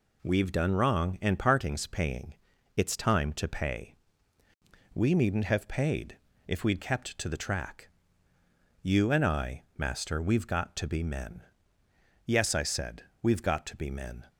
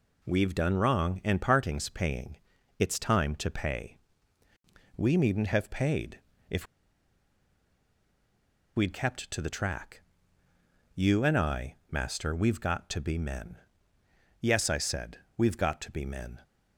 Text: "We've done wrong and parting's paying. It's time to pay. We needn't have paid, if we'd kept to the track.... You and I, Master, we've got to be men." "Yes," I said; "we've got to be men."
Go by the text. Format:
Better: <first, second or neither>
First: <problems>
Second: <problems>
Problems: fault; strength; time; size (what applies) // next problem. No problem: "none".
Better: first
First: none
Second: pauses between "if" and "we'd"; strong; at 6.6 s; 2.1 s long